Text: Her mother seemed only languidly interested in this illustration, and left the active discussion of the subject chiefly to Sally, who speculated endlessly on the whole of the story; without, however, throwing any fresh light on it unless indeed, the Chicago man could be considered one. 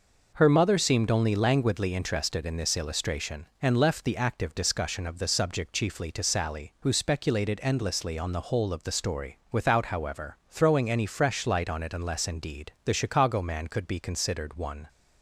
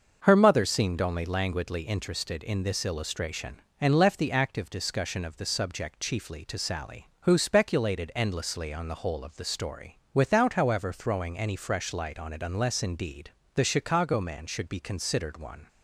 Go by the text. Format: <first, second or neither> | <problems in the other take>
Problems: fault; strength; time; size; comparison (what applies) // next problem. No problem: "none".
first | starts louder than the rest; until 1.2 s; 6 dB // says "should" for "could"; at 14.4 s